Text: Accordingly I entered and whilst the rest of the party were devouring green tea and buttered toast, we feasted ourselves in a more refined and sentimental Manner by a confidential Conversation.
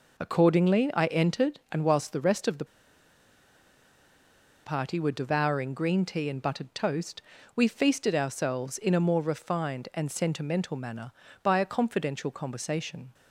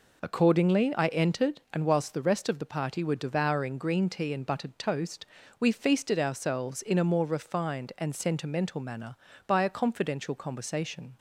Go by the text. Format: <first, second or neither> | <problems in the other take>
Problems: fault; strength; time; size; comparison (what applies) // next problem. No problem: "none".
second | pauses between "the" and "party"; strong; at 2.6 s; 1.9 s long